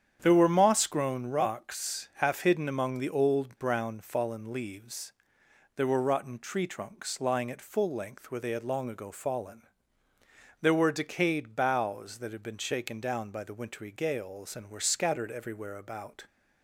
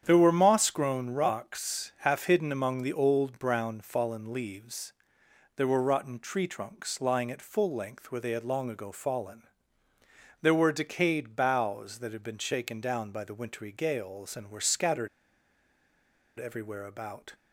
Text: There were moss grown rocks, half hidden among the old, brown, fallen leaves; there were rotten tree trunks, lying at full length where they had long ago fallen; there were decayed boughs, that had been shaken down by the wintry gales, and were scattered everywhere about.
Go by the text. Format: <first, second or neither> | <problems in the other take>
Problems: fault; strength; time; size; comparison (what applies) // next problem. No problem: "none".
first | starts louder than the rest; strong; until 1.0 s; 8.5 dB; strong in the first // pauses between "scattered" and "everywhere"; strong; at 15.0 s; 1.3 s long